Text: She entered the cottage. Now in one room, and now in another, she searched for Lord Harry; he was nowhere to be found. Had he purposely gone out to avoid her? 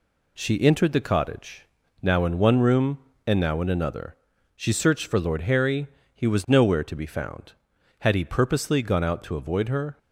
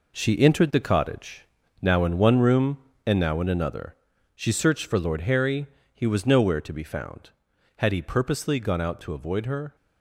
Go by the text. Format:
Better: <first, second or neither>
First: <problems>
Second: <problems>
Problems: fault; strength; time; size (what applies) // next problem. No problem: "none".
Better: first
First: none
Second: gets quieter; strong; throughout; 8.5 dB